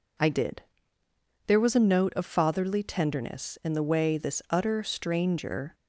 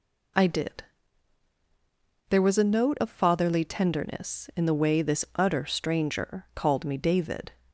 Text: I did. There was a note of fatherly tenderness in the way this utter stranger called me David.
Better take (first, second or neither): second